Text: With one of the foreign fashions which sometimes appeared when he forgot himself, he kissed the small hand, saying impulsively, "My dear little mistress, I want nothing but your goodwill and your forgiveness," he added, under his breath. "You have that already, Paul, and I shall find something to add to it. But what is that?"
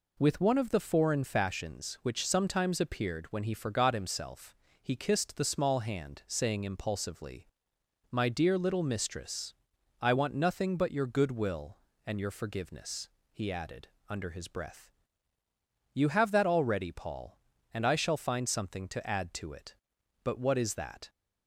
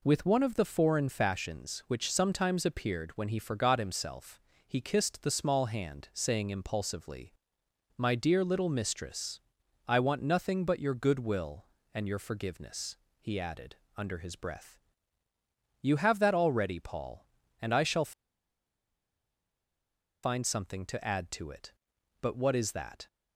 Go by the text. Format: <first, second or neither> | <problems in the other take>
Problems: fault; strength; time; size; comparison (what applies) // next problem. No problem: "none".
first | pauses between "shall" and "find"; strong; at 18.1 s; 2.1 s long